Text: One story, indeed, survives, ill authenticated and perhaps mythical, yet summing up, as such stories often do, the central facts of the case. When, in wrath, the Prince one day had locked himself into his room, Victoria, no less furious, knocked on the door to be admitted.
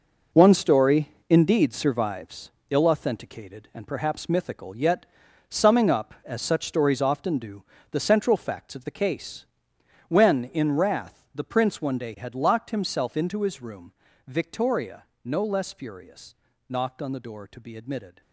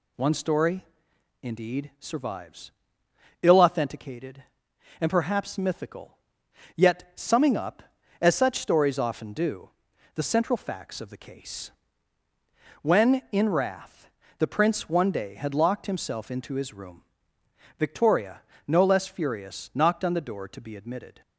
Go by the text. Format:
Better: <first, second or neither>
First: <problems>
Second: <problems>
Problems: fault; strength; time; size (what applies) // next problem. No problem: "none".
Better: second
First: gets quieter; strong; throughout; 10 dB // pauses between "yet" and "summing"; at 5.0 s; 0.42 s long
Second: none